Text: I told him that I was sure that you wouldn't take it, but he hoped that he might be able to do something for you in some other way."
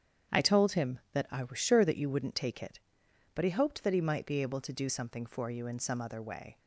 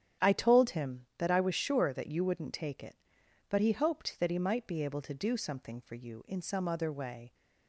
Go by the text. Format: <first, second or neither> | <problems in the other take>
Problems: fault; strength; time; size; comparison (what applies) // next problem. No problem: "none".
neither | starts louder than the rest; strong; the same in both